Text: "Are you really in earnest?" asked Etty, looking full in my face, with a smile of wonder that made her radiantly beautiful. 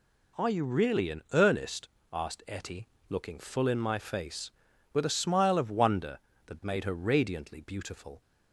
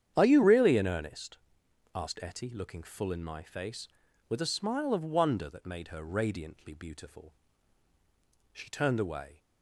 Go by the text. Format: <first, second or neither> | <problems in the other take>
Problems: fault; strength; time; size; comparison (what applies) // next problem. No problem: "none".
first | starts louder than the rest; strong; until 1.1 s; 9 dB // goes on to say "She turned away"; noticeable; from 8.5 s on; 0.87 s long